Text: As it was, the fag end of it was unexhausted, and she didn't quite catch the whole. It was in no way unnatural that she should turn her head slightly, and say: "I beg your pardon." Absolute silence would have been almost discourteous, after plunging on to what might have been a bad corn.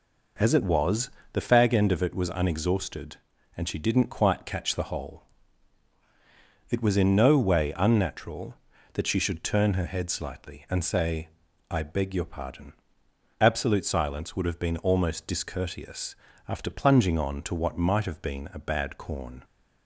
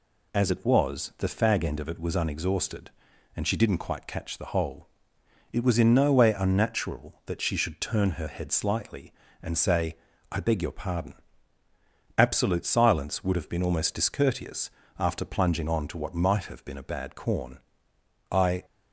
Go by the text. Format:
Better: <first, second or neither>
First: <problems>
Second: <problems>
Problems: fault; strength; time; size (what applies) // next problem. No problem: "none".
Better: first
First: none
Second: goes on to say "I"; slight; from 18.3 s on; 0.34 s long